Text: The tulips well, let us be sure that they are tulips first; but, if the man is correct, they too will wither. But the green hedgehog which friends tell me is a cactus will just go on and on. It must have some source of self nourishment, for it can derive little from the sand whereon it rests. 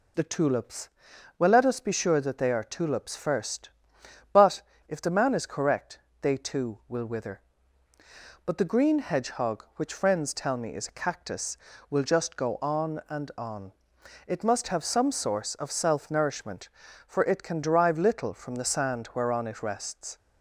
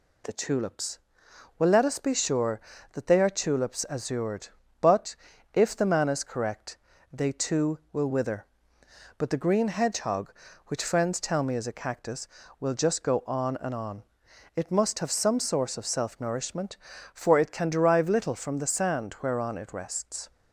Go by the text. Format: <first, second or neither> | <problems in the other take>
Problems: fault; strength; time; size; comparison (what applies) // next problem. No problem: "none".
first | pauses between "tulips" and "well"; noticeable; at 0.9 s; 0.62 s long; noticeable in the first // says "azured" for "first"; at 3.9 s